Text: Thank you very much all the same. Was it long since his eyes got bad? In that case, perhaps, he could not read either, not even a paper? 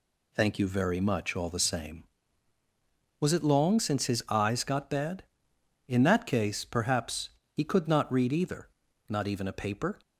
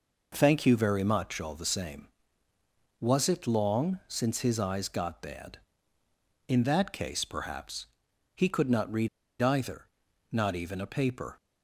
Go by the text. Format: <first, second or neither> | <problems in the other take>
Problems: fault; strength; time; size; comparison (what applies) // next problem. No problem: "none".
first | pauses between "read" and "either"; slight; at 9.0 s; 0.33 s long